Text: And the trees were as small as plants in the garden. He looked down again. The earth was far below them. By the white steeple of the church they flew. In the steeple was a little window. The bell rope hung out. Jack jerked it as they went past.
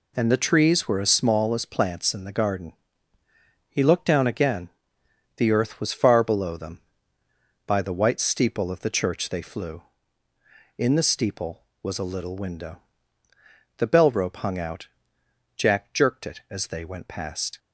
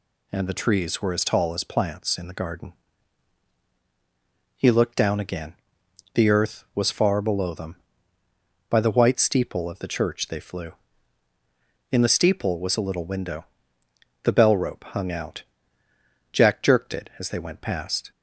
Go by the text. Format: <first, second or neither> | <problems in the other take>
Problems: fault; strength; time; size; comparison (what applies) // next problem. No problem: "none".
first | says "tall" for "small"; at 1.2 s